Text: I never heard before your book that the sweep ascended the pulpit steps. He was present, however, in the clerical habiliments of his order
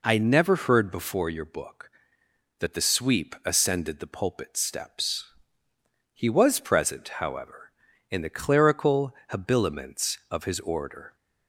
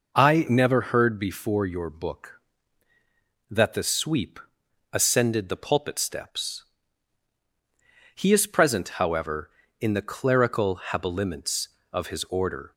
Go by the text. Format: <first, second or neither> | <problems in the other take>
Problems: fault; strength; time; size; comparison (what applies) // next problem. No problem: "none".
first | pauses between "sweep" and "ascended"; noticeable; at 4.4 s; 0.50 s long // says "is" for "was"; at 8.3 s